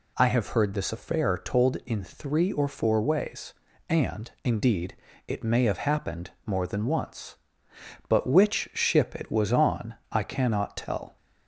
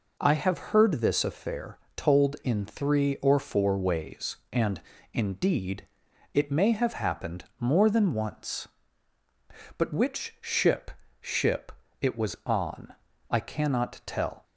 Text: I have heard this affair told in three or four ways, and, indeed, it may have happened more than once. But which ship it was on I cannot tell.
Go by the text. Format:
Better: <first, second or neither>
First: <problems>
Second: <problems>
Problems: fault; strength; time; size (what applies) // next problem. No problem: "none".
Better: first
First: pauses between "happened" and "more"; slight; at 6.3 s; 0.16 s long // pauses between "on" and "I"; slight; at 9.9 s; 0.18 s long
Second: pauses between "affair" and "told"; slight; at 1.7 s; 0.18 s long // pauses between "happened" and "more"; slight; at 7.4 s; 0.16 s long // says "ship" twice; at 11.2 s // pauses between "on" and "I"; slight; at 12.9 s; 0.36 s long